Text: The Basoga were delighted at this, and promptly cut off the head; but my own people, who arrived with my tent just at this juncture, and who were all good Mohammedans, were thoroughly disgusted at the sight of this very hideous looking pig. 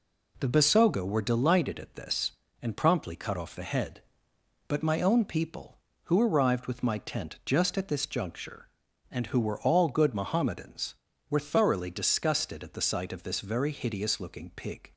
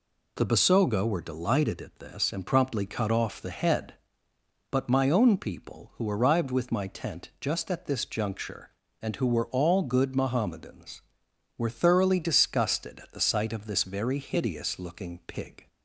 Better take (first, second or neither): neither